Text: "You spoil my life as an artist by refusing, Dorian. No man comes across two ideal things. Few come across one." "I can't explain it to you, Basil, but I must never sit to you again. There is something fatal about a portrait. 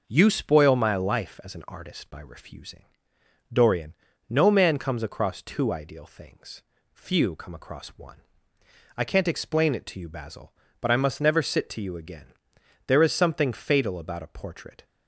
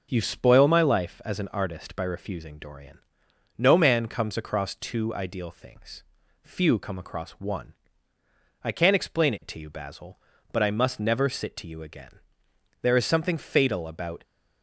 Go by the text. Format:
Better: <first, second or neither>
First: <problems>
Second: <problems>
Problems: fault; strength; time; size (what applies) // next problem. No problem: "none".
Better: first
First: none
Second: starts louder than the rest; until 1.1 s; 6.5 dB // stops before "a portrait"; at 14.2 s